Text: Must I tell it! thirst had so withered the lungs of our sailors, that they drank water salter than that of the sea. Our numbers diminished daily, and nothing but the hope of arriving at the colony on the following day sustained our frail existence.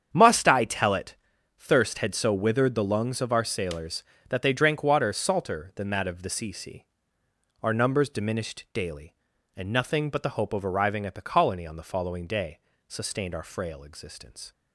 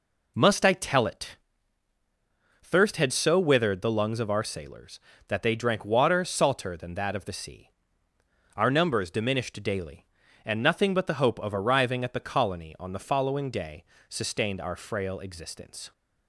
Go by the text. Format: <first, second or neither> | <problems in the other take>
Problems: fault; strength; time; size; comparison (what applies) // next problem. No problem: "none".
second | starts louder than the rest; strong; until 1.1 s; 8 dB // says "sea" twice; at 6.5 s // pauses between "day" and "sustained"; slight; at 12.5 s; 0.30 s long; slight in the second